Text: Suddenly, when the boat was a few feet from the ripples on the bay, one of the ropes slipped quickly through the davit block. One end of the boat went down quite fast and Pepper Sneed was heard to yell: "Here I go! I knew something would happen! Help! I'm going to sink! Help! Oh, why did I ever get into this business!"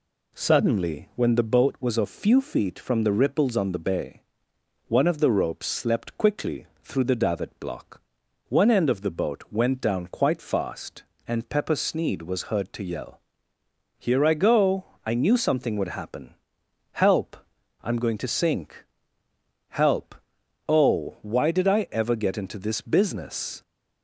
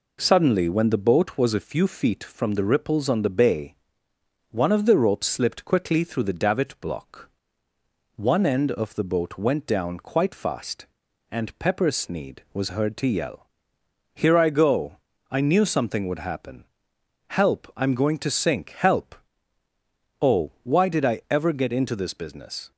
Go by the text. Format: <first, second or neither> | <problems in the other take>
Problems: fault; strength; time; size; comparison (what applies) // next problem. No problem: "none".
second | says "slept" for "slipped"; at 5.6 s // pauses between "quickly" and "through"; slight; at 6.6 s; 0.16 s long